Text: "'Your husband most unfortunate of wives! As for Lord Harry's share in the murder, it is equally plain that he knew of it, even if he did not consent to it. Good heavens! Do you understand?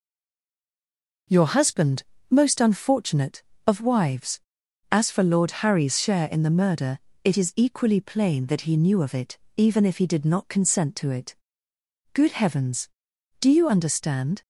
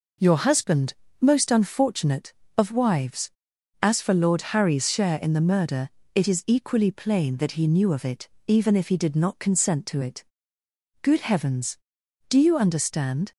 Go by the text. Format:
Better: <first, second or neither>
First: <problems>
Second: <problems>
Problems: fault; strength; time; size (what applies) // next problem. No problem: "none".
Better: second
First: stays silent before the first word; noticeable; until 1.2 s; 1.2 s long // pauses between "husband" and "most"; slight; at 2.0 s; 0.28 s long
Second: pauses between "husband" and "most"; slight; at 0.9 s; 0.28 s long